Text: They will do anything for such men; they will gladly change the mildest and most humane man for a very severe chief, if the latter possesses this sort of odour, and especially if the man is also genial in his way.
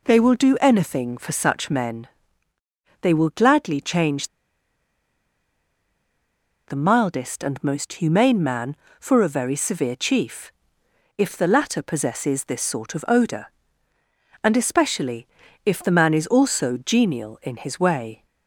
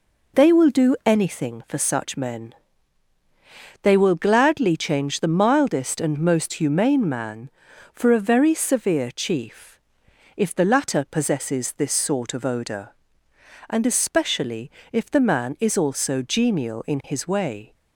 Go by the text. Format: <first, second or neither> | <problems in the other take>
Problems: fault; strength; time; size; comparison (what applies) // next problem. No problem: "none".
second | pauses between "change" and "the"; strong; at 4.2 s; 2.3 s long // pauses between "especially" and "if"; at 15.2 s; 0.40 s long; slight in the second